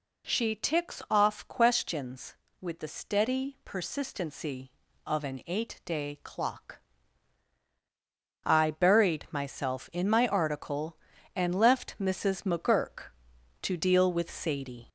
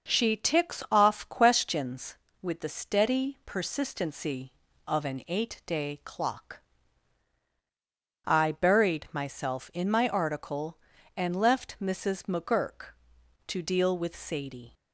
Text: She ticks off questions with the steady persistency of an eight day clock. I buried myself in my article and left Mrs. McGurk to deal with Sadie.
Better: second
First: gets louder; slight; throughout; 3 dB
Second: none

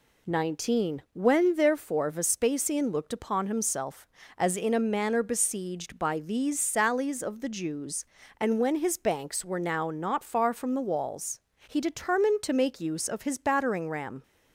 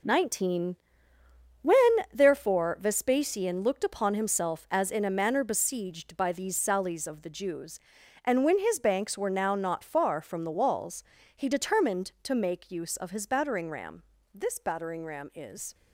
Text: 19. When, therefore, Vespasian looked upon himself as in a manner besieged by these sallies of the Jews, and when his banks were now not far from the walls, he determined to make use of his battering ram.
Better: first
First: none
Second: goes on to say "This battering ram is"; from 14.3 s on; 1.4 s long

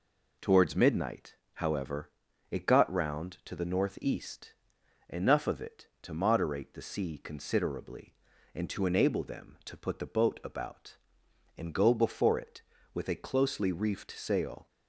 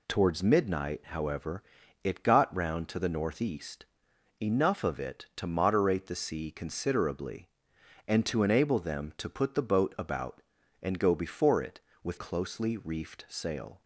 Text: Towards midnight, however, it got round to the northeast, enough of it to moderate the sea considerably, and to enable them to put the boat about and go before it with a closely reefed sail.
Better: first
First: none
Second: skips "a"; at 12.1 s

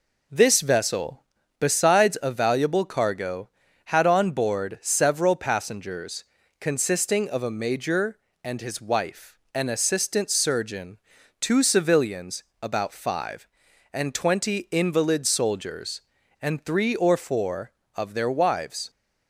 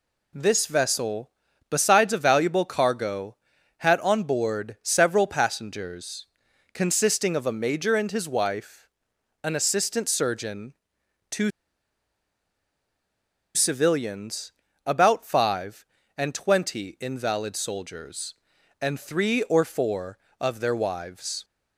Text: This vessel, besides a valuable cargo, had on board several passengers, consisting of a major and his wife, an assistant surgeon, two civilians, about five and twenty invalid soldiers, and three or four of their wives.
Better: first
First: none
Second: pauses between "two" and "civilians"; strong; at 11.5 s; 2.0 s long

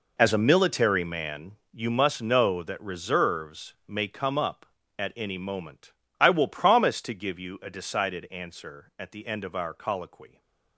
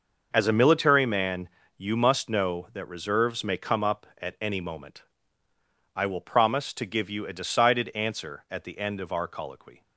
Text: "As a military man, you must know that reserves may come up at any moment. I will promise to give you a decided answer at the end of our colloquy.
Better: second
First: gets quieter; strong; throughout; 13.5 dB // stays silent after the last word; slight; from 10.2 s on; 0.5 s long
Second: none

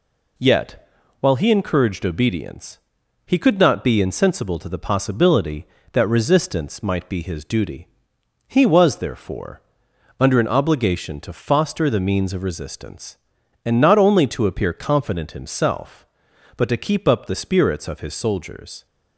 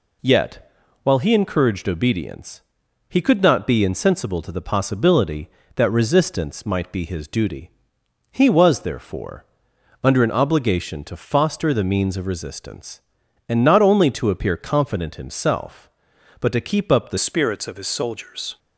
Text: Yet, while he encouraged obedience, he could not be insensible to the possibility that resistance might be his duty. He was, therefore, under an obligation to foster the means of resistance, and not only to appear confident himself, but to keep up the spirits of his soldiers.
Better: first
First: none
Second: changes voice at "spirits"; from 17.1 s on; 1.4 s long

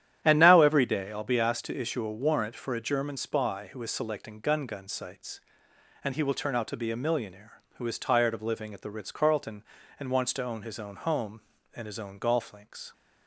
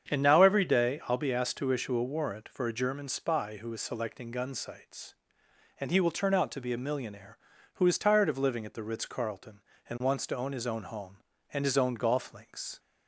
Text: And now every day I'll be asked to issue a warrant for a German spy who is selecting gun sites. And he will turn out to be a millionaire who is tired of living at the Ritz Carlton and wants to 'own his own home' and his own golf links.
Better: second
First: starts louder than the rest; strong; until 1.2 s; 10.5 dB // says "gun" twice; at 4.6 s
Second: starts louder than the rest; strong; until 1.1 s; 8 dB

